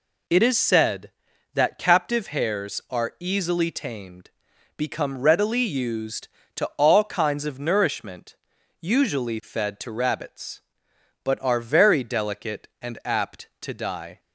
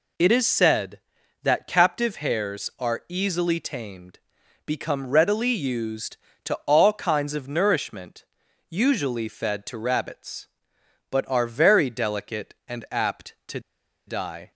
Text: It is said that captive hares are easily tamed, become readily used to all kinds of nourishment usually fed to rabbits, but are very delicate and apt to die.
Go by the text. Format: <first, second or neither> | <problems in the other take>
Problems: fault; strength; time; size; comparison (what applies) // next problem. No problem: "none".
first | pauses between "nourishment" and "usually"; at 8.2 s; 0.44 s long; also in the first // pauses between "to" and "die"; noticeable; at 13.5 s; 0.47 s long